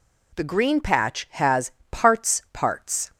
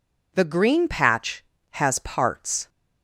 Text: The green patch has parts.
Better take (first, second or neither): second